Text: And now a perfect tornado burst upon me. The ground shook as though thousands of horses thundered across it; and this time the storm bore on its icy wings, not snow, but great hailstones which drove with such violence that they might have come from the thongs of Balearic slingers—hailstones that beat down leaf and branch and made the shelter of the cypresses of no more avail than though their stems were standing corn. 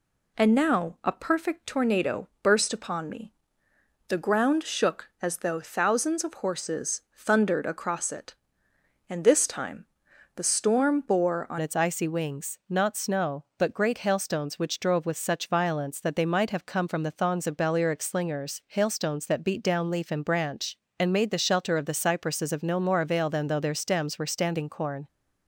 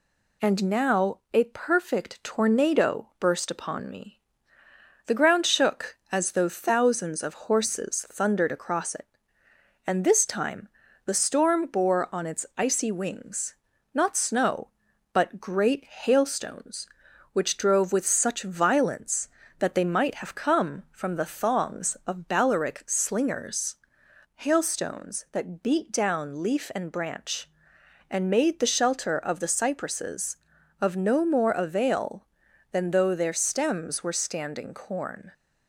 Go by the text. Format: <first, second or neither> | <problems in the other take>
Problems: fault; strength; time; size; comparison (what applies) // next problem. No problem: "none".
second | pauses between "time" and "the"; noticeable; at 9.8 s; 0.50 s long; also in the second // changes voice at "its"; from 11.6 s on; 13.4 s long